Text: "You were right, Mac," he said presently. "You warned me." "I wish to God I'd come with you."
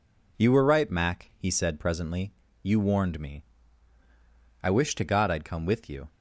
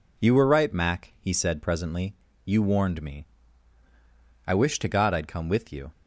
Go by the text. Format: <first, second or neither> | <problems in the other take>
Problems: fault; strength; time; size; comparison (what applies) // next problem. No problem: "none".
neither | none